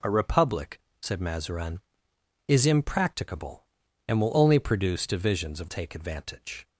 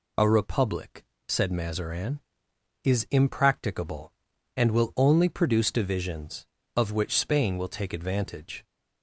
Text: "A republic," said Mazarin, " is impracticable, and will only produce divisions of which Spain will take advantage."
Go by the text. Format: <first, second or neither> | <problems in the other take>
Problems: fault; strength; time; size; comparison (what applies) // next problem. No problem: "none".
second | skips "which Spain will"; at 5.6 s